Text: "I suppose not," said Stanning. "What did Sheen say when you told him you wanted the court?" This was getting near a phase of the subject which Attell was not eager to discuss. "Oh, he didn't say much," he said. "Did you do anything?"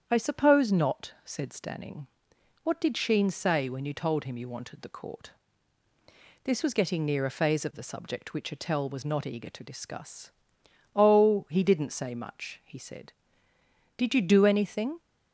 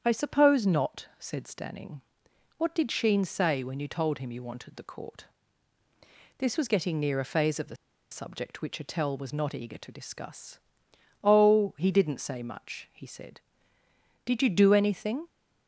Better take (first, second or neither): first